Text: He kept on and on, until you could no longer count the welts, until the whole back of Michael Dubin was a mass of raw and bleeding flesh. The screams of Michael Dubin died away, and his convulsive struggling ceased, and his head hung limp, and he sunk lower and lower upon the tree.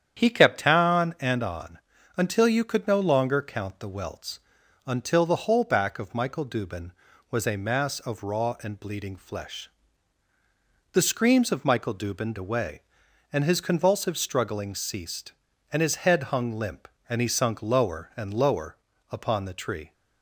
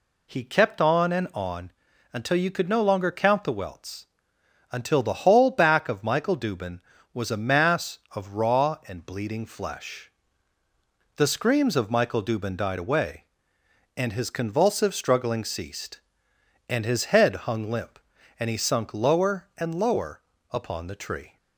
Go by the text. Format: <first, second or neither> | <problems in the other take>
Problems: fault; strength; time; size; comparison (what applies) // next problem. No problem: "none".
second | starts louder than the rest; strong; until 1.2 s; 9 dB // skips "died"; at 12.3 s // pauses between "lower" and "upon"; at 18.7 s; 0.38 s long; slight in the second